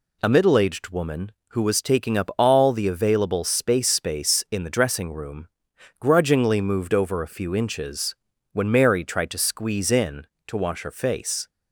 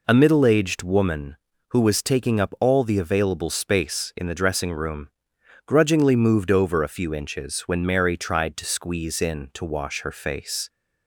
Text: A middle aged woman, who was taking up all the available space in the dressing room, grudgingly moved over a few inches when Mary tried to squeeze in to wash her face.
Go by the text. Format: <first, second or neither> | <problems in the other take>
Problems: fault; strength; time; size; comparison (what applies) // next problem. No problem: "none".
second | says "space" twice; at 3.8 s // pauses between "inches" and "when"; slight; at 8.1 s; 0.34 s long